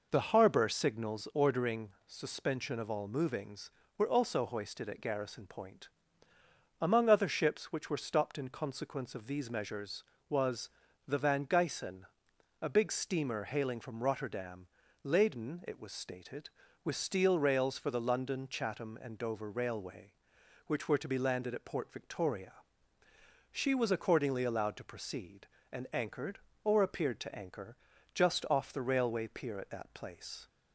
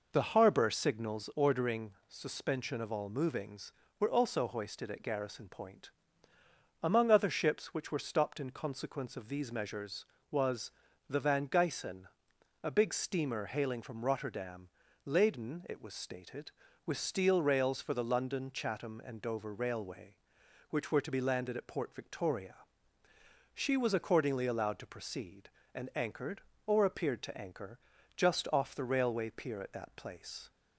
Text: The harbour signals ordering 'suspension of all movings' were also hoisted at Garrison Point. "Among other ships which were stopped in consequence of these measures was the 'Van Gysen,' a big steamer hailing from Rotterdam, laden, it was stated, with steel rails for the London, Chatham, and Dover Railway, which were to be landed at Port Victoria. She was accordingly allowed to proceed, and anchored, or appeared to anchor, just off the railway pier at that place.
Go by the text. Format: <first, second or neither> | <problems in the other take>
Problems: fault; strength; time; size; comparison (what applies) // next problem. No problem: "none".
neither | pauses between "ordering" and "suspension"; slight; the same in both // pauses between "was" and "the"; the same in both